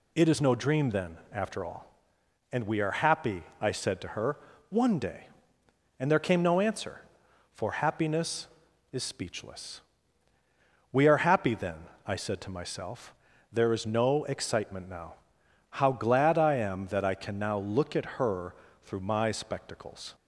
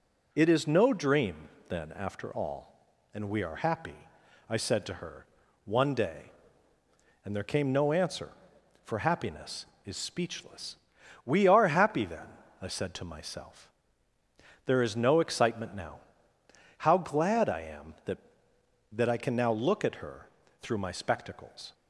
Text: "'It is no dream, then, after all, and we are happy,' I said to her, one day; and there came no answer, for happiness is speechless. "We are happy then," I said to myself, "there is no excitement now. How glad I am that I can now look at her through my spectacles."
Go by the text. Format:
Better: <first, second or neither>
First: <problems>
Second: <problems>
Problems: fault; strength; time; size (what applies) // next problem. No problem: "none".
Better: first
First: pauses between "her" and "through"; slight; at 18.5 s; 0.30 s long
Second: says "that" twice; at 18.9 s // pauses between "her" and "through"; slight; at 20.2 s; 0.34 s long